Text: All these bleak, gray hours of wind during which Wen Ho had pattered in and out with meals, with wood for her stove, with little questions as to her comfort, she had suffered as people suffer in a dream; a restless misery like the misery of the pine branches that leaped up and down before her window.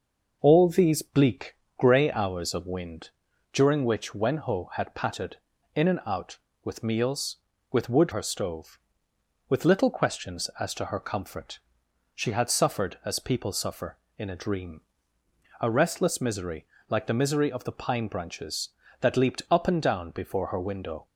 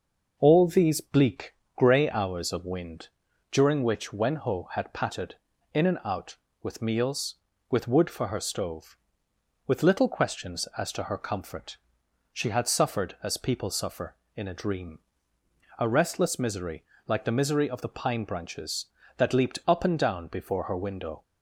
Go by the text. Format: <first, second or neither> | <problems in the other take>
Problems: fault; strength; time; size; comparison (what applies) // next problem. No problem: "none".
second | pauses between "wind" and "during"; at 3.0 s; 0.44 s long; also in the second // skips "for"; at 8.1 s // pauses between "misery" and "like"; slight; at 16.6 s; 0.24 s long; slight in the second